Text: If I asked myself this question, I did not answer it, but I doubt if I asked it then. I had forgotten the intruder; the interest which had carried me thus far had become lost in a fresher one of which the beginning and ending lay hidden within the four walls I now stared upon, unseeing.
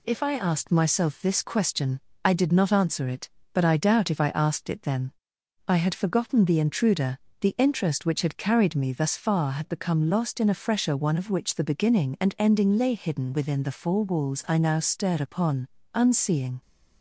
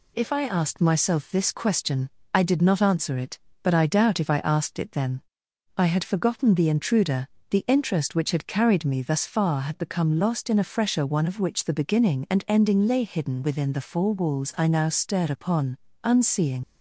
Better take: first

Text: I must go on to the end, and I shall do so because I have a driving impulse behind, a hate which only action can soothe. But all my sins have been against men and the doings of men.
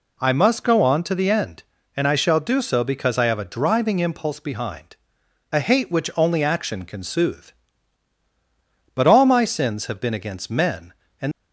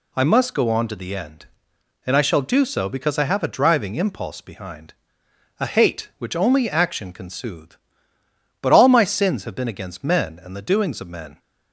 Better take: second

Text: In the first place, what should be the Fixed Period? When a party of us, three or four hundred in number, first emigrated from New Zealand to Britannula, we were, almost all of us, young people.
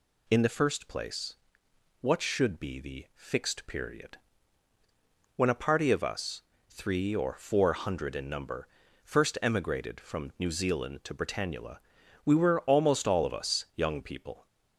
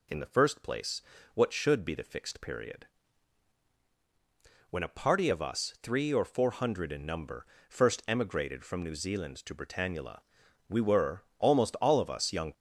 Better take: first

